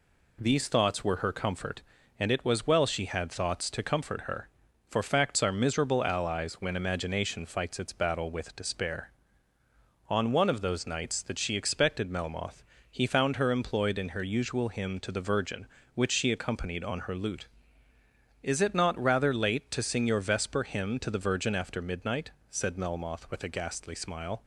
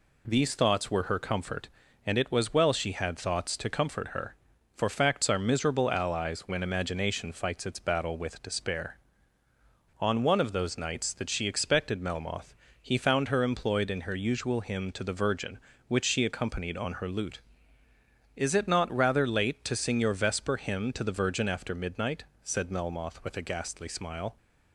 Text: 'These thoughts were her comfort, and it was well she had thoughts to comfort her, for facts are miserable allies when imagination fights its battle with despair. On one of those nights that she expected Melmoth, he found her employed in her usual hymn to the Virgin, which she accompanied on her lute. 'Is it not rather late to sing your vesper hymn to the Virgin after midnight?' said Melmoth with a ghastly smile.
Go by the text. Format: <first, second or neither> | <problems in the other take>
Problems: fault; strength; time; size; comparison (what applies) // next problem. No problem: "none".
neither | none